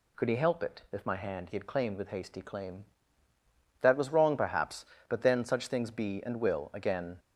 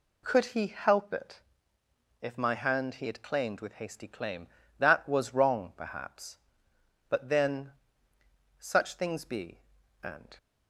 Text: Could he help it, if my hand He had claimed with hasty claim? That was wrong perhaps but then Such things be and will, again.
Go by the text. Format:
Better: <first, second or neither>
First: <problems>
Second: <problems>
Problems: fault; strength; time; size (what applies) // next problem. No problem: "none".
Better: first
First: none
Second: pauses between "then" and "Such"; noticeable; at 7.7 s; 0.87 s long // stops before "will again"; at 10.3 s